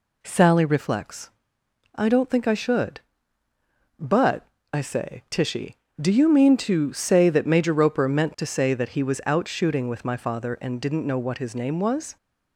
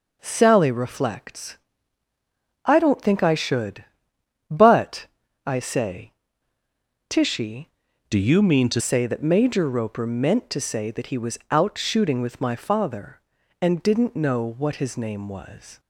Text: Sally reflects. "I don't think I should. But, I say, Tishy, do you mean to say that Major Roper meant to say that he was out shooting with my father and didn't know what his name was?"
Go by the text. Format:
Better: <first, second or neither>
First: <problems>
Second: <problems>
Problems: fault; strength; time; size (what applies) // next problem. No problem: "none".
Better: first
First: none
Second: changes voice from "do" to "to"; from 8.0 to 8.8 s; 0.8 s long